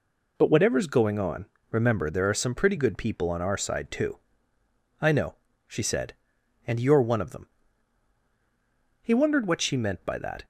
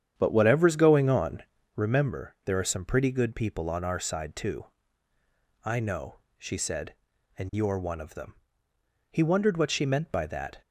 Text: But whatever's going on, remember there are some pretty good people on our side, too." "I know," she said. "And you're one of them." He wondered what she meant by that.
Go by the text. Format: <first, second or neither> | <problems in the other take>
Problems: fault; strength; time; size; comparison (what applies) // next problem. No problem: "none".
first | starts louder than the rest; strong; until 1.9 s; 8.5 dB